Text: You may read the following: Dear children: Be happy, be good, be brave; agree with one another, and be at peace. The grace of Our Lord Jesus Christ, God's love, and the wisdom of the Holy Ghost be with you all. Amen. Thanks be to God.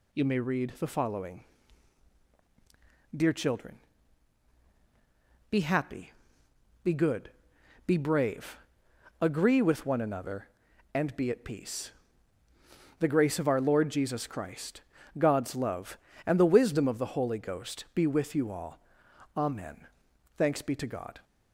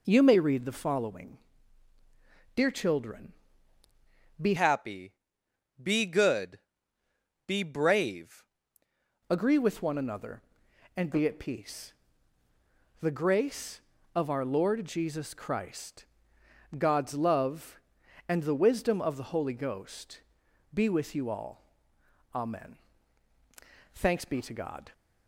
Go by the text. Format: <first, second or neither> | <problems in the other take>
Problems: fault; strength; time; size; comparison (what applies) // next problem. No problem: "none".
first | changes voice from "happy" to "brave"; from 4.5 to 8.4 s; 3.9 s long // pauses between "Ghost" and "be"; noticeable; at 20.2 s; 0.52 s long